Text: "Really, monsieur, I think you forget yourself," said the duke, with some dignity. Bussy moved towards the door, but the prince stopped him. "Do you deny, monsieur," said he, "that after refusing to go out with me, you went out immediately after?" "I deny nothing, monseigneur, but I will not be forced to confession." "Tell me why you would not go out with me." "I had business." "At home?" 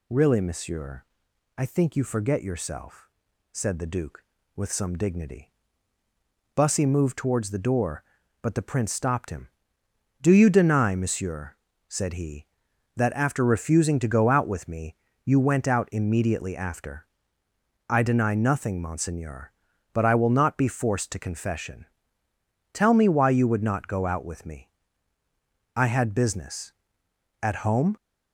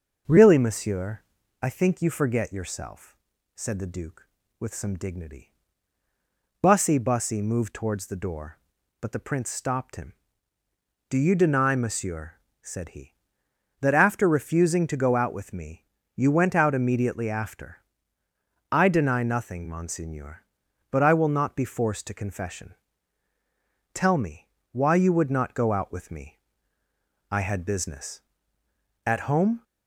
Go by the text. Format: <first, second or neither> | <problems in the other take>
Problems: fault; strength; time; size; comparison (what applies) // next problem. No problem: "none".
first | starts louder than the rest; noticeable; until 1.6 s; 6 dB // says "Bussy" twice; at 6.9 s // pauses between "me" and "why"; slight; at 24.4 s; 0.24 s long